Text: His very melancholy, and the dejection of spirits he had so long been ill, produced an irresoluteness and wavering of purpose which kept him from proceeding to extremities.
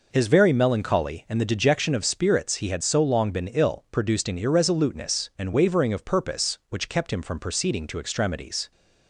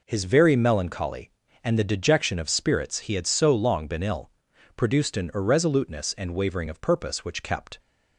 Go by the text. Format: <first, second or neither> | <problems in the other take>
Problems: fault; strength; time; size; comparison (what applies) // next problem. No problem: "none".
first | stops before "him from proceeding to extremities"; at 7.7 s